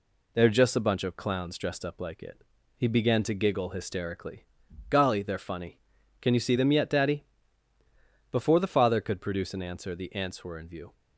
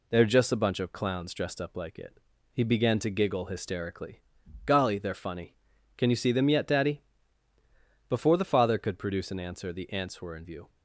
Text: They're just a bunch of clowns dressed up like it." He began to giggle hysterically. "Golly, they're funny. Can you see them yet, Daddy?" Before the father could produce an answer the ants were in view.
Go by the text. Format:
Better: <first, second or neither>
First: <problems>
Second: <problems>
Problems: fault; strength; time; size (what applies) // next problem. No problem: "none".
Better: neither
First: none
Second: none